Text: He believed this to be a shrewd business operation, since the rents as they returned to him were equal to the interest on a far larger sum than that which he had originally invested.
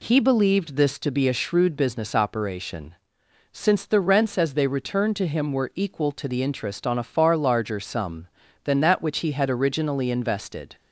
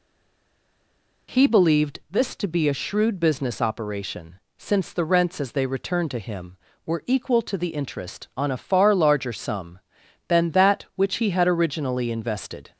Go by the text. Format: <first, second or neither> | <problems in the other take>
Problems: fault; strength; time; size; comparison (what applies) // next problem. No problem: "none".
first | stays silent before the first word; noticeable; until 1.2 s; 1.2 s long